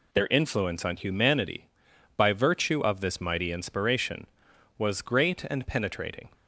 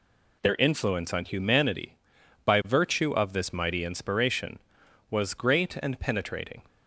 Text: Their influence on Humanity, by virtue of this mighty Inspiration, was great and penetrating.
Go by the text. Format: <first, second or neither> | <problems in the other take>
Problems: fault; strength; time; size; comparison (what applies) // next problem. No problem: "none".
neither | none